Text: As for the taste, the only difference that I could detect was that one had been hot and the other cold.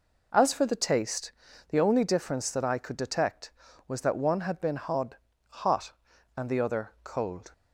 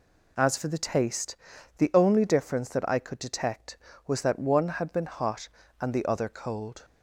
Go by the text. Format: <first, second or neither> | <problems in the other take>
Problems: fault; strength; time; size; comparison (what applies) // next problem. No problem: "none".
second | says "hot" twice; at 5.4 s